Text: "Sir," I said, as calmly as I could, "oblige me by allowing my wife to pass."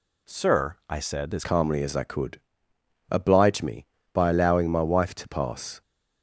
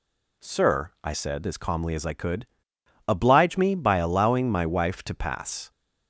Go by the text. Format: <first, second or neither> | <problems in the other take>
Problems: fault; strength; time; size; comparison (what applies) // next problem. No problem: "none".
second | changes voice at "calmly"; from 1.4 s on; 4.4 s long